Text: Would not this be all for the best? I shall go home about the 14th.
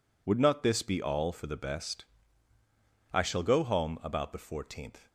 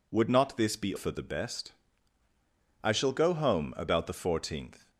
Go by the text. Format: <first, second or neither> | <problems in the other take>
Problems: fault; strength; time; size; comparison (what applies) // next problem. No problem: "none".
first | skips "all"; at 0.9 s